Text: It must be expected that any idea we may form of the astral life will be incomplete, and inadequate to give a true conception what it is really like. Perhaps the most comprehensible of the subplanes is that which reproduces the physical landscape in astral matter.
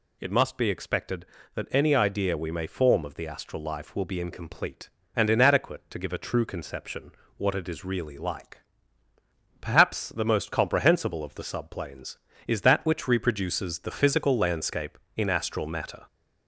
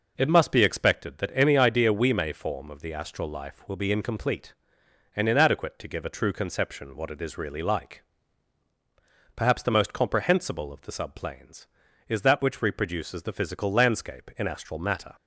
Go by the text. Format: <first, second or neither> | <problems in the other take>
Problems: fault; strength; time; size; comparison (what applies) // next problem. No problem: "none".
second | gets louder; slight; throughout; 2.5 dB // pauses between "conception" and "what"; slight; at 7.1 s; 0.26 s long